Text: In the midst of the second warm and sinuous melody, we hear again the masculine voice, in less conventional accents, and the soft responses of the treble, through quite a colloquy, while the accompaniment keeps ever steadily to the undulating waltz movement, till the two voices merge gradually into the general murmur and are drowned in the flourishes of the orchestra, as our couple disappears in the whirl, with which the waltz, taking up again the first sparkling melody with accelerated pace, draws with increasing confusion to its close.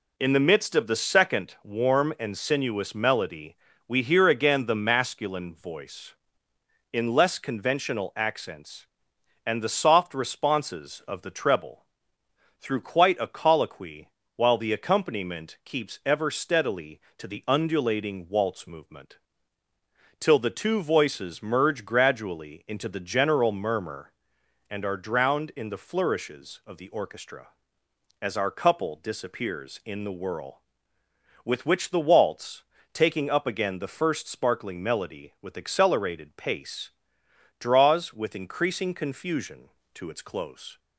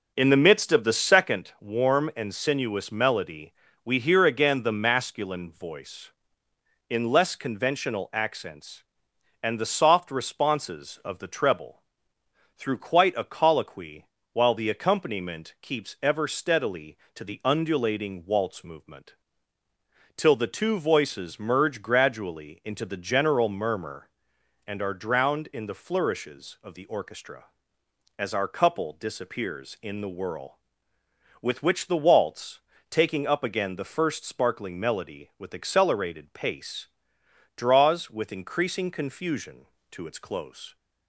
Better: first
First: none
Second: starts louder than the rest; noticeable; until 1.2 s; 5 dB

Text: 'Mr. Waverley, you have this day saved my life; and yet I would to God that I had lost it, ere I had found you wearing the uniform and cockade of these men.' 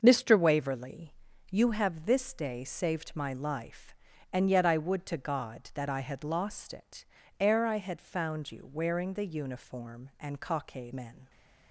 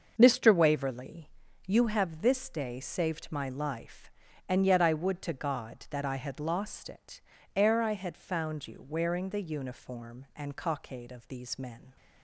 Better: second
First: starts louder than the rest; until 1.0 s; 6.5 dB // skips "of these"; at 10.9 s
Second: starts louder than the rest; until 1.1 s; 6.5 dB

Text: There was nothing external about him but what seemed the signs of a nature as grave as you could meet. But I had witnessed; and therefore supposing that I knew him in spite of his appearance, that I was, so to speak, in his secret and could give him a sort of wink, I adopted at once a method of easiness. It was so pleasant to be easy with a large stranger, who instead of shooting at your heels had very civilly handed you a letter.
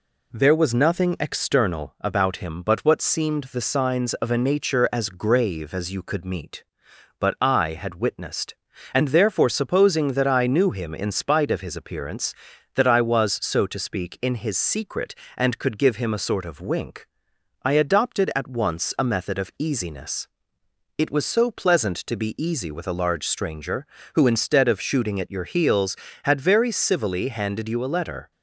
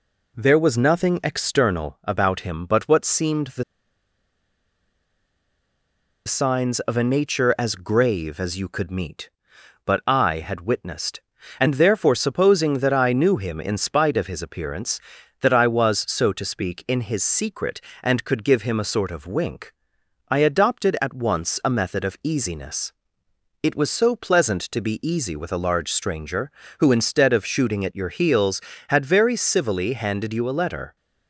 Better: first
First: none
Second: pauses between "the" and "signs"; strong; at 3.6 s; 2.6 s long

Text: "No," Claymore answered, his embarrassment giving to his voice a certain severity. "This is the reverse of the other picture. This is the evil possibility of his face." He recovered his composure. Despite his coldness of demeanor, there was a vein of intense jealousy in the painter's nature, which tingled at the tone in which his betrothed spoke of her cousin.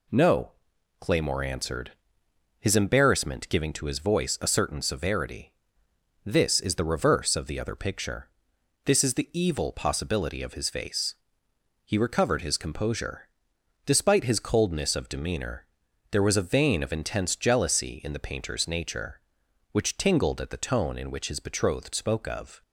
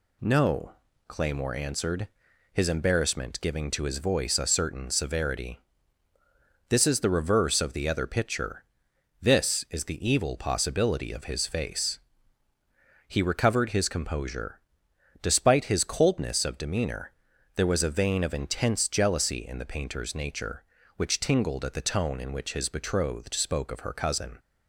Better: second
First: stops before "her cousin"; at 22.6 s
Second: none

